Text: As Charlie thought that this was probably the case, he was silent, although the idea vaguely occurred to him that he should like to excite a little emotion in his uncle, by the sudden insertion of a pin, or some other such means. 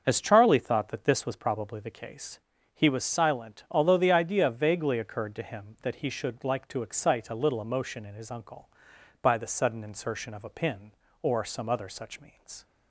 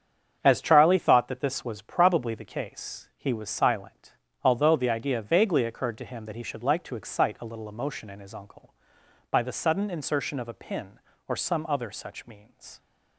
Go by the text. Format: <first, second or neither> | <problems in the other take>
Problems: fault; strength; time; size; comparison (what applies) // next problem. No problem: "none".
neither | starts louder than the rest; the same in both